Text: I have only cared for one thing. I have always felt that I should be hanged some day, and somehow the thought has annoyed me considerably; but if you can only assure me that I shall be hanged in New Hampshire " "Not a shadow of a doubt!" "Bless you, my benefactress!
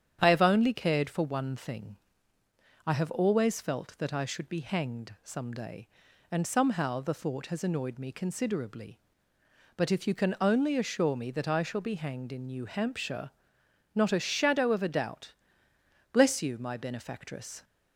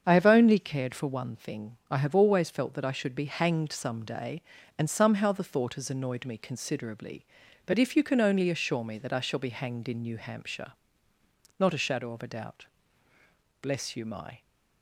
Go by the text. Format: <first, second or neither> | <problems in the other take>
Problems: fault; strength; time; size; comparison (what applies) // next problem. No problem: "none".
first | starts louder than the rest; strong; until 1.0 s; 7 dB; strong in the first // stops before "benefactress"; at 14.4 s